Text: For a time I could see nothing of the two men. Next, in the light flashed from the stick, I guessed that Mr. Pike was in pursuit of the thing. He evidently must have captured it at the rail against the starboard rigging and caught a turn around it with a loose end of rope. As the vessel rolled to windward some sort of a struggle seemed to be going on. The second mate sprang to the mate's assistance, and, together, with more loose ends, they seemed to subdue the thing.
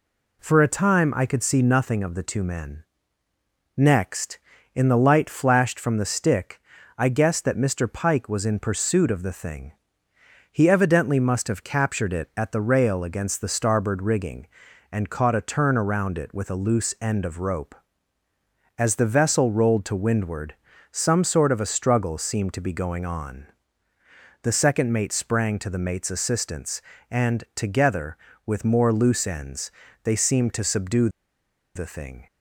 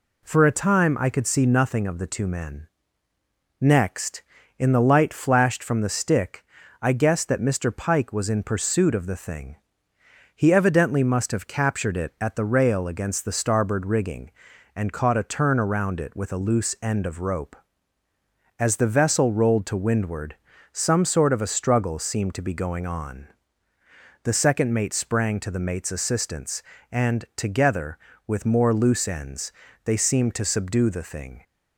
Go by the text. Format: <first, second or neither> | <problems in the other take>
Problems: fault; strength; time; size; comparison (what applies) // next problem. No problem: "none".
second | pauses between "windward" and "some"; slight; at 20.5 s; 0.36 s long; slight in the second // pauses between "subdue" and "the"; noticeable; at 31.0 s; 0.67 s long